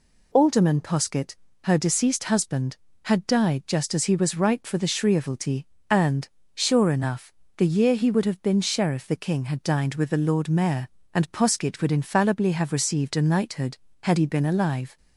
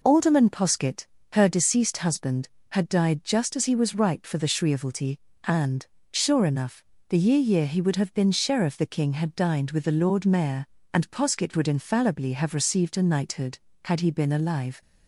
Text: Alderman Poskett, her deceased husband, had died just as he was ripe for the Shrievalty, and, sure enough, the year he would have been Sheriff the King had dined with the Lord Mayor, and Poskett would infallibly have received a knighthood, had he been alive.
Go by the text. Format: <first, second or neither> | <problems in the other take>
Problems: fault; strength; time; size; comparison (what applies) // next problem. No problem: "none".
first | says "year" twice; at 7.3 s